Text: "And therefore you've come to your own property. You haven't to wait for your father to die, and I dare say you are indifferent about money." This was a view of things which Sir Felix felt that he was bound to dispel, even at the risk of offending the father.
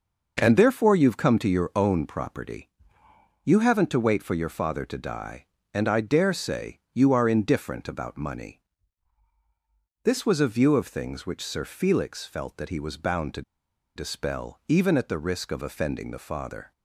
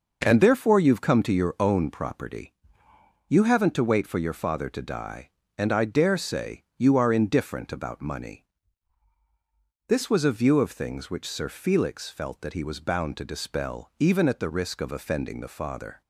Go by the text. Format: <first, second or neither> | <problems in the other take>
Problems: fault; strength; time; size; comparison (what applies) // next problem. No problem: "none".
second | pauses between "say" and "you"; slight; at 6.7 s; 0.16 s long; slight in the second // pauses between "to" and "dispel"; noticeable; at 13.4 s; 0.53 s long